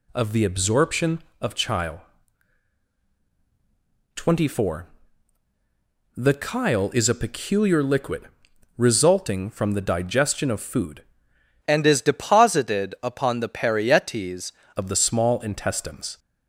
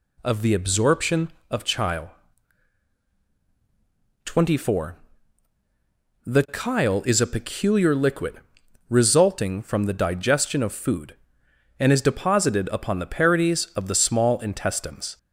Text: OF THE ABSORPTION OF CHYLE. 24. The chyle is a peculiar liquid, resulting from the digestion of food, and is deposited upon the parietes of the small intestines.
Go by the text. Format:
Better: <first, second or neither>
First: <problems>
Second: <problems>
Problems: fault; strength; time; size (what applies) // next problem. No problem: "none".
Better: second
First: changes voice from "and" to "parietes"; from 11.6 to 14.5 s; 2.9 s long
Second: none